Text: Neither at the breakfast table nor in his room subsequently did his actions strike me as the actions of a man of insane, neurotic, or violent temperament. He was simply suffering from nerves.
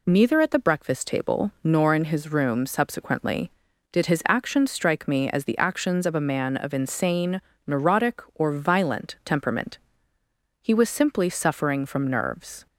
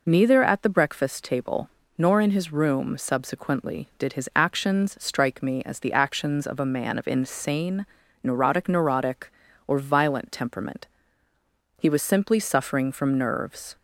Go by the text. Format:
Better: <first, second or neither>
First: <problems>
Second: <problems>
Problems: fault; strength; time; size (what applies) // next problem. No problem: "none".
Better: first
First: none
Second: pauses between "table" and "nor"; slight; at 1.6 s; 0.30 s long // says "neurotic" twice; at 8.7 s